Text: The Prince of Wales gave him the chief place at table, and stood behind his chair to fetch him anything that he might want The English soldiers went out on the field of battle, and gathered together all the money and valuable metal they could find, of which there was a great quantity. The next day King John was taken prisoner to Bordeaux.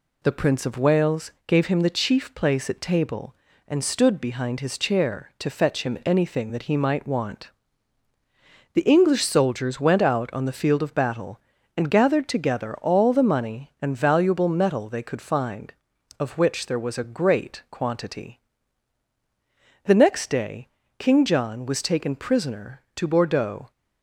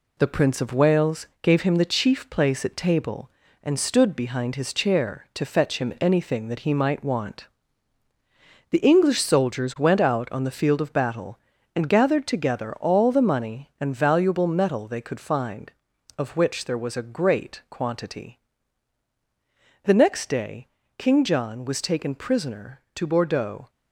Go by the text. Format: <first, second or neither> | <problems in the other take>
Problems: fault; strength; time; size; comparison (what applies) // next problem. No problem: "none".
first | gets quieter; noticeable; throughout; 4.5 dB // pauses between "Wales" and "gave"; slight; at 1.2 s; 0.16 s long; slight in the first // pauses between "want" and "The"; at 7.4 s; 1.2 s long; also in the first // pauses between "day" and "King"; slight; at 20.6 s; 0.32 s long; slight in the first